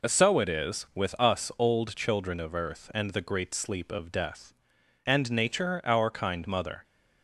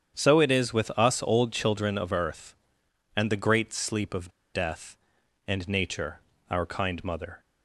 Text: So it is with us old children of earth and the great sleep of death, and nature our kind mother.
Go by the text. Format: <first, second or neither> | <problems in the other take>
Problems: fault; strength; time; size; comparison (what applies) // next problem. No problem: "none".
first | starts louder than the rest; strong; until 1.2 s; 8.5 dB // pauses between "of" and "death"; slight; at 4.3 s; 0.22 s long // pauses between "nature" and "our"; slight; at 6.1 s; 0.28 s long